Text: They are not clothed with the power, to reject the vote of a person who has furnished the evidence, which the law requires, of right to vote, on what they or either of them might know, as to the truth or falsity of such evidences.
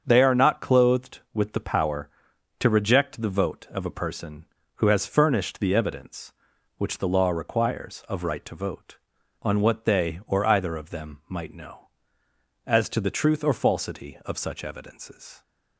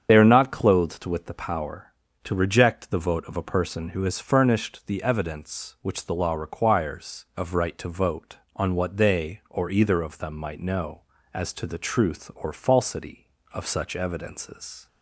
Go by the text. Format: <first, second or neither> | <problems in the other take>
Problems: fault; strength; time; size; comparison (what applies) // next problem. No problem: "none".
first | loses the start of "They"; at 0.0 s; 45 ms // starts louder than the rest; strong; until 1.1 s; 8 dB; also in the first